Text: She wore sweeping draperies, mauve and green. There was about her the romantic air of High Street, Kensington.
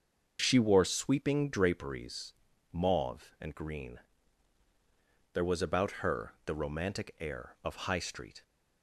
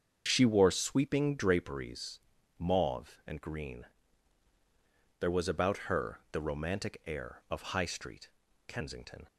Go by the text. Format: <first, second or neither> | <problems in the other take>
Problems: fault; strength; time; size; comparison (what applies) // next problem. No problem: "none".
second | starts louder than the rest; until 1.4 s; 6.5 dB; also in the second // stops before "Kensington"; at 8.4 s